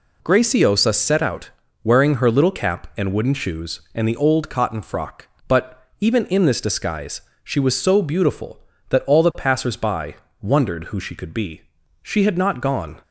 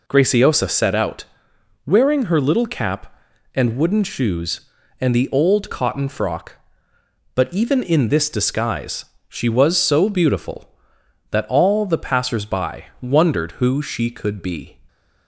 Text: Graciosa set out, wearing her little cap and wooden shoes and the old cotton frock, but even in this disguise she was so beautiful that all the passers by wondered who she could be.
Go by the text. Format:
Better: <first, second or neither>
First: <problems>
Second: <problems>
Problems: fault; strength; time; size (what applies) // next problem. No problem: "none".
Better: second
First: pauses between "but" and "even"; slight; at 5.8 s; 0.16 s long // pauses between "disguise" and "she"; slight; at 7.2 s; 0.22 s long // pauses between "by" and "wondered"; slight; at 10.1 s; 0.24 s long // goes on to say "She had not gone"; noticeable; from 12.0 s on; 1.0 s long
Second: pauses between "disguise" and "she"; slight; at 9.0 s; 0.24 s long